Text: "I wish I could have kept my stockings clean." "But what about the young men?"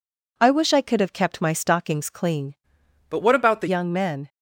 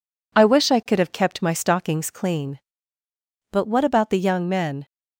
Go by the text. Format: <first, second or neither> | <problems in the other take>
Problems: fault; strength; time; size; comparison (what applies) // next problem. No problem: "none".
second | changes voice from "But" to "the"; from 3.0 to 3.6 s; 0.6 s long